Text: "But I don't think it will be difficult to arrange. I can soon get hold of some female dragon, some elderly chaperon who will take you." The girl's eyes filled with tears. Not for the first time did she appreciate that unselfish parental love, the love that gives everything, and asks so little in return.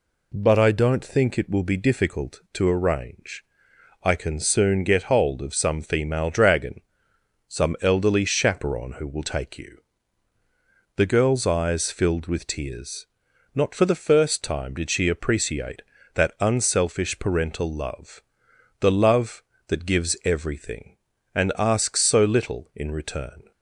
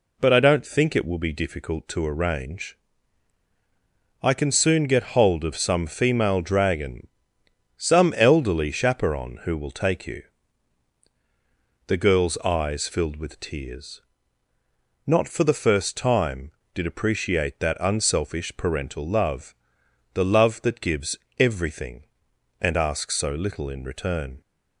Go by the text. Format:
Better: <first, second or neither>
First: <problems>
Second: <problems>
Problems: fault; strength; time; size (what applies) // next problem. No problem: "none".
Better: first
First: none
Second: skips "she"; at 16.8 s // pauses between "gives" and "everything"; slight; at 21.1 s; 0.22 s long